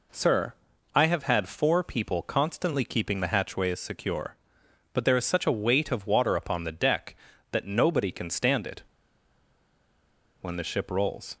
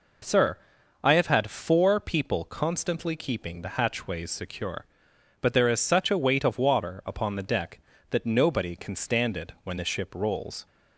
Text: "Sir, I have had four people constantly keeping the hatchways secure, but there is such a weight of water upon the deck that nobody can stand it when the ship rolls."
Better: second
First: pauses between "it" and "when"; strong; at 8.8 s; 1.5 s long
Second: none

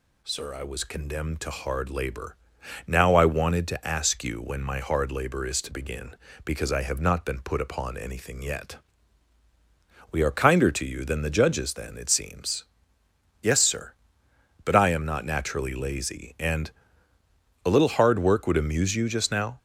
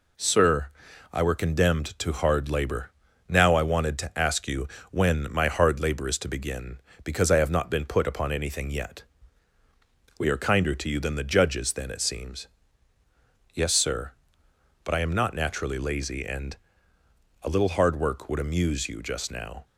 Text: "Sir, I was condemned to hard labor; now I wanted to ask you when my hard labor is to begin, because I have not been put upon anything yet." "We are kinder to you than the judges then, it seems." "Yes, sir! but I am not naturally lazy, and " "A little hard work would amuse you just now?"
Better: first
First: none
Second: says "were" for "was"; at 1.2 s // pauses between "you" and "when"; slight; at 4.6 s; 0.24 s long

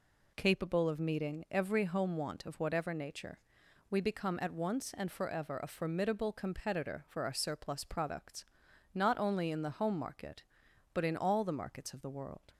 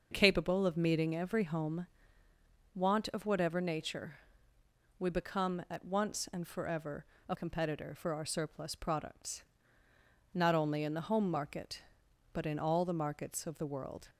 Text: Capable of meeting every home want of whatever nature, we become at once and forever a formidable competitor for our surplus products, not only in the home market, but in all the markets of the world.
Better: first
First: none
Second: pauses between "home" and "want"; noticeable; at 1.8 s; 0.88 s long // pauses between "forever" and "a"; slight; at 7.0 s; 0.24 s long // skips "formidable"; at 7.3 s

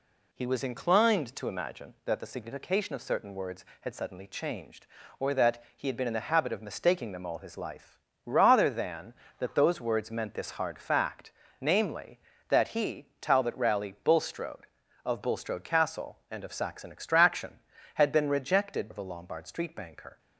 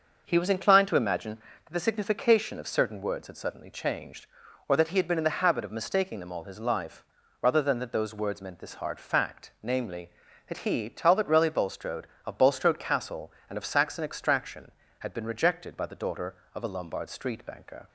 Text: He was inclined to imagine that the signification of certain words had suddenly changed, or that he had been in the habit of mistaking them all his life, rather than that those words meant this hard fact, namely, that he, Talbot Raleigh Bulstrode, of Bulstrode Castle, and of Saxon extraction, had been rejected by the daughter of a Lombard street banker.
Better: second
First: skips "by the daughter"; at 18.8 s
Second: none

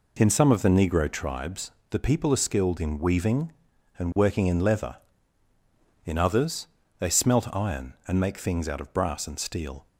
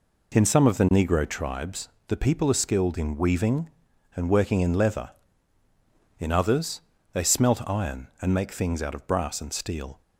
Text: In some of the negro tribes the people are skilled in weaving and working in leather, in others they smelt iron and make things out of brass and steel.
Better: neither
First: pauses between "tribes" and "the"; slight; at 1.6 s; 0.22 s long // pauses between "others" and "they"; slight; at 6.6 s; 0.32 s long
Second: pauses between "tribes" and "the"; slight; at 1.8 s; 0.22 s long // pauses between "others" and "they"; slight; at 6.8 s; 0.32 s long

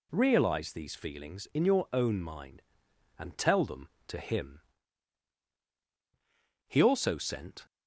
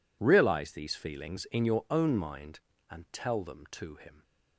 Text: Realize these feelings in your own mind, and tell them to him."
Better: second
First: goes on to say "He also sent"; noticeable; from 6.6 s on; 1.0 s long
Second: none

